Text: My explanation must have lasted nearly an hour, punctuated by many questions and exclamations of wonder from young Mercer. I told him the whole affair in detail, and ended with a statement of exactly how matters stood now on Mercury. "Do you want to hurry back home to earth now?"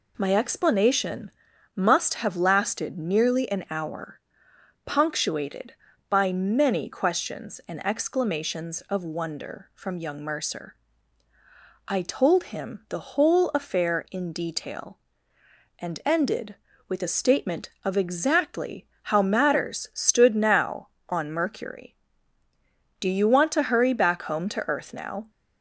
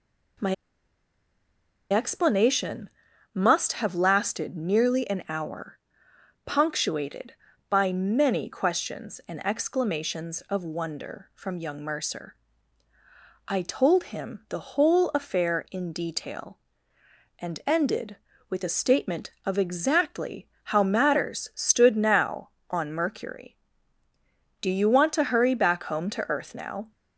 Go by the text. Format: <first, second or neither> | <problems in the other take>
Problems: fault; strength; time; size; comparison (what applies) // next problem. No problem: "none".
first | pauses between "My" and "explanation"; strong; at 0.5 s; 1.3 s long // pauses between "explanation" and "must"; at 2.8 s; 0.44 s long; also in the first // pauses between "exactly" and "how"; slight; at 20.4 s; 0.16 s long; slight in the first